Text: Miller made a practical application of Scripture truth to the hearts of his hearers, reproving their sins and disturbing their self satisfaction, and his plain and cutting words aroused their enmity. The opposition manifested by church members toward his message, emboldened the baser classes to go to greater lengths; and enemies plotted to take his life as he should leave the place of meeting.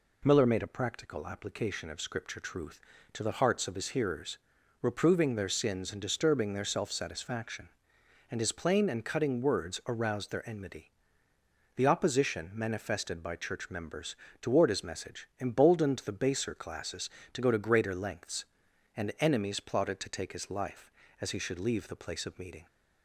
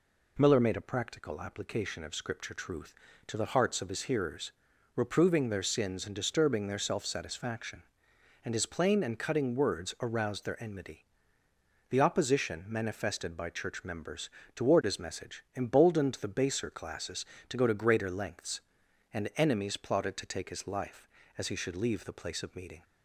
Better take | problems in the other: neither | pauses between "members" and "toward"; slight; the same in both

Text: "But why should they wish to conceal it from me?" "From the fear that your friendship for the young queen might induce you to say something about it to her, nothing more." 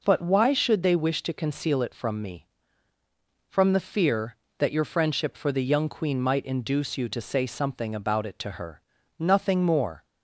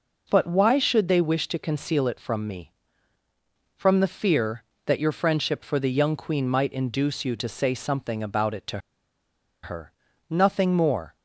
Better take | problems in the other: first | pauses between "to" and "her"; noticeable; at 8.7 s; 0.84 s long

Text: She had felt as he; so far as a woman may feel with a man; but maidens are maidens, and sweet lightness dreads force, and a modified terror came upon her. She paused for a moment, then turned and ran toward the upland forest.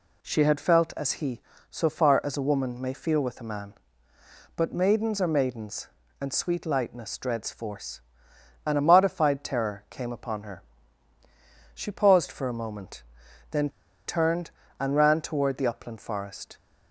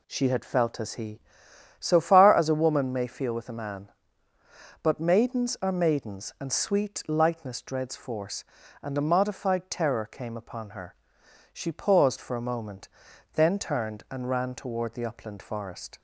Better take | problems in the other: second | pauses between "then" and "turned"; at 13.6 s; 0.39 s long

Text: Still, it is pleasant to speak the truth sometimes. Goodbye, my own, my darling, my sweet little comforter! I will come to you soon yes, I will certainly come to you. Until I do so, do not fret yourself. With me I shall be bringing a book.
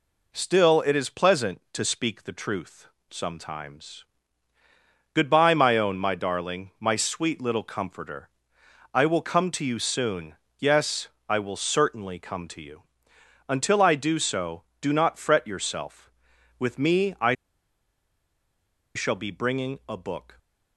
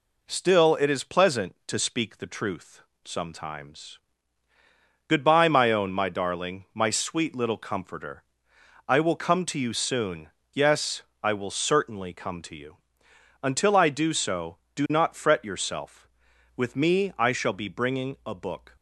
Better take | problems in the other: second | pauses between "truth" and "sometimes"; slight; at 2.8 s; 0.24 s long; slight in the second // pauses between "soon" and "yes"; slight; at 10.3 s; 0.24 s long; slight in the second // pauses between "I" and "shall"; strong; at 17.3 s; 1.6 s long

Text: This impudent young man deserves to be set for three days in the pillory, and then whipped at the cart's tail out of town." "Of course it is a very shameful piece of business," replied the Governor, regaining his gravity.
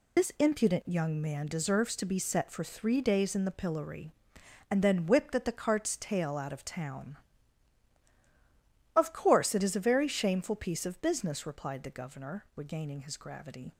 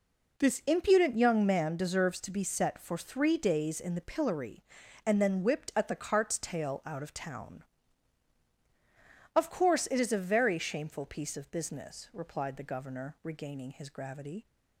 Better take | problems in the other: second | loses the start of "This"; at 0.1 s; 50 ms

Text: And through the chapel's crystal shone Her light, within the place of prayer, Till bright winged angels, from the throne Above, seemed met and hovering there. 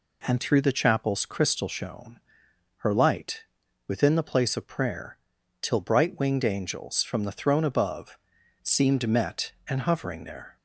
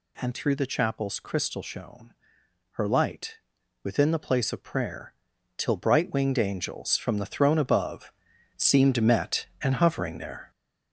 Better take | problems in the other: first | gets louder; noticeable; throughout; 6 dB // pauses between "shone" and "Her"; noticeable; at 2.1 s; 0.58 s long; noticeable in the first

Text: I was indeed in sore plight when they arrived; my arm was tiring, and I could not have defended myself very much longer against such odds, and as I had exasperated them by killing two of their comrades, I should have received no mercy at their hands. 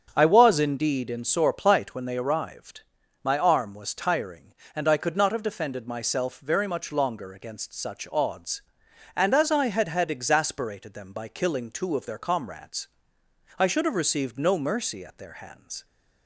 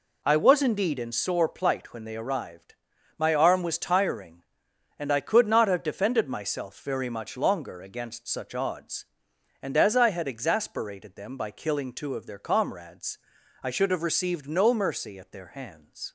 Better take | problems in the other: second | starts louder than the rest; strong; until 1.1 s; 7.5 dB // says "had" twice; at 9.8 s

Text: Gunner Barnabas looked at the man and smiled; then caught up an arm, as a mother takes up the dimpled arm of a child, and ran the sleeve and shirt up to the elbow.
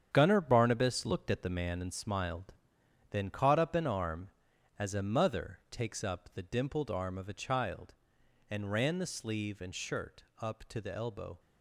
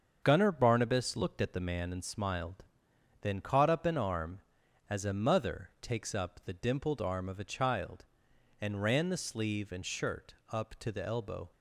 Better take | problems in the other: second | gets quieter; strong; throughout; 9.5 dB // starts louder than the rest; strong; until 1.1 s; 8.5 dB; also in the second // pauses between "shirt" and "up"; slight; at 10.2 s; 0.18 s long; slight in the second

